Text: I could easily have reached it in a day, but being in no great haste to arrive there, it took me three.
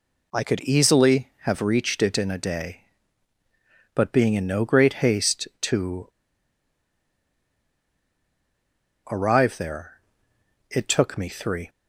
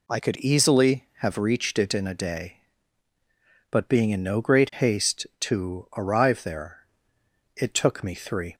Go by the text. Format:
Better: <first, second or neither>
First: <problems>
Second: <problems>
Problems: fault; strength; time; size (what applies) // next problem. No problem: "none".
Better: second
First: pauses between "to" and "arrive"; strong; at 6.0 s; 3.0 s long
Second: none